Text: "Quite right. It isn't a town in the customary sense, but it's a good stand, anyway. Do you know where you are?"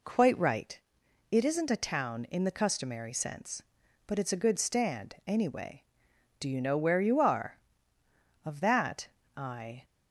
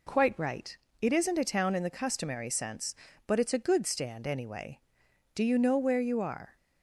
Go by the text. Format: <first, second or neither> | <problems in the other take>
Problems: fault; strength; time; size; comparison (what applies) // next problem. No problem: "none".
second | goes on to say "Of that I"; from 8.4 s on; 1.4 s long